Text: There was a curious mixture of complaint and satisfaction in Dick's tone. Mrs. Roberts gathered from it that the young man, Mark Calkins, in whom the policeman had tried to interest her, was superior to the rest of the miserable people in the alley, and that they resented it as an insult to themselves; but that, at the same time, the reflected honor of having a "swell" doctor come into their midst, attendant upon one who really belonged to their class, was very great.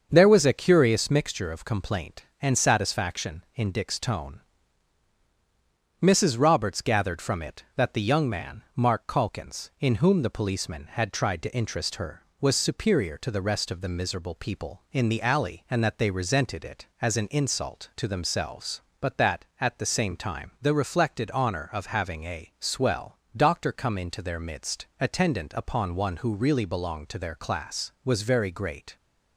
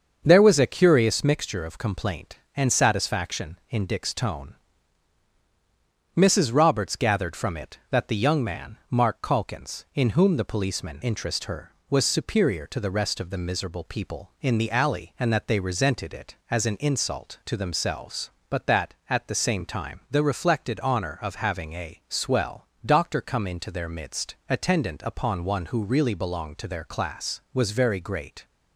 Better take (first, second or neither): first